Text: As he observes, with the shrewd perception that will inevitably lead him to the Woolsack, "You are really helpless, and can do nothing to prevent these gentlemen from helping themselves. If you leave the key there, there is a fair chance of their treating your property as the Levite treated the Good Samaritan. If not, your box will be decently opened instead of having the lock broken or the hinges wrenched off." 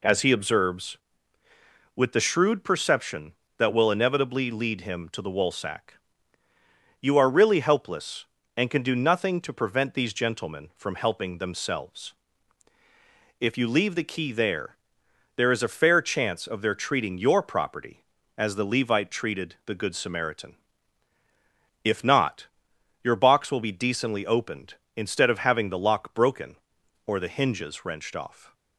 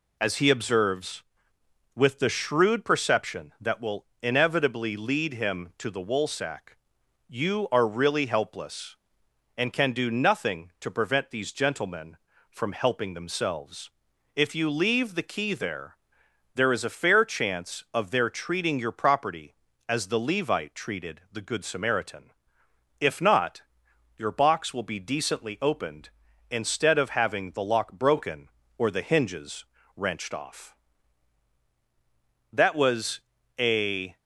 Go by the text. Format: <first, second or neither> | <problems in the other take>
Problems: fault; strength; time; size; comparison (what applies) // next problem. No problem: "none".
first | pauses between "will" and "inevitably"; slight; at 4.0 s; 0.16 s long // pauses between "hinges" and "wrenched"; slight; at 29.6 s; 0.32 s long // goes on to say "That was a"; from 32.5 s on; 1.6 s long